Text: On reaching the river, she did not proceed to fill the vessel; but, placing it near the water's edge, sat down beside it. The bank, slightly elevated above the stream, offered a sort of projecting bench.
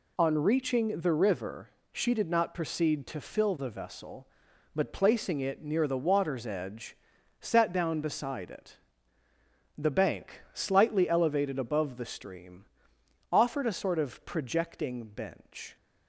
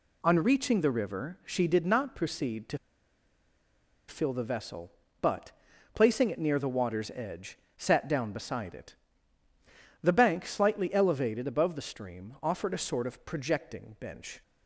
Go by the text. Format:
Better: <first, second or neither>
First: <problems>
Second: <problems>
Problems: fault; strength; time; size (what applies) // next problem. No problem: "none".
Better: first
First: none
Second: pauses between "to" and "fill"; strong; at 2.7 s; 1.3 s long